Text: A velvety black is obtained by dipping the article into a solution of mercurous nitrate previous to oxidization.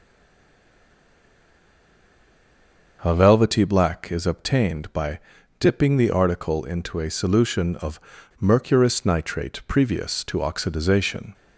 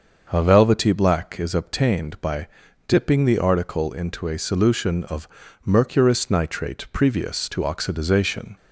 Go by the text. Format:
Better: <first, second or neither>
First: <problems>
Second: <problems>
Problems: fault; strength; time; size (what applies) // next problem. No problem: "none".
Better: second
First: stays silent before the first word; strong; until 2.9 s; 2.9 s long // starts louder than the rest; until 4.0 s; 6.5 dB // pauses between "by" and "dipping"; at 5.1 s; 0.38 s long // pauses between "of" and "mercurous"; at 7.9 s; 0.41 s long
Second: starts louder than the rest; until 1.3 s; 6.5 dB // pauses between "by" and "dipping"; at 2.4 s; 0.38 s long // pauses between "of" and "mercurous"; at 5.2 s; 0.38 s long